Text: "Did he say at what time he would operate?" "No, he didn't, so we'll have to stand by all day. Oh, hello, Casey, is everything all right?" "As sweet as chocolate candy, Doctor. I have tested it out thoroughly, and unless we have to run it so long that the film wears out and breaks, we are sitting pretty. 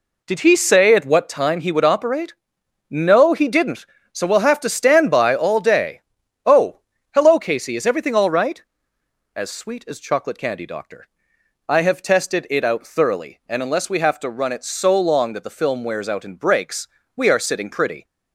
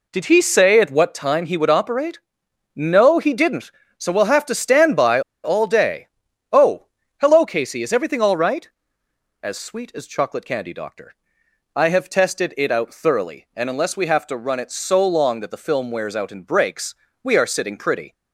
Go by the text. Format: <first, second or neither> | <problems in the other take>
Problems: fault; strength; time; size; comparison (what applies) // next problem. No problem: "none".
first | pauses between "by" and "all"; slight; at 5.1 s; 0.23 s long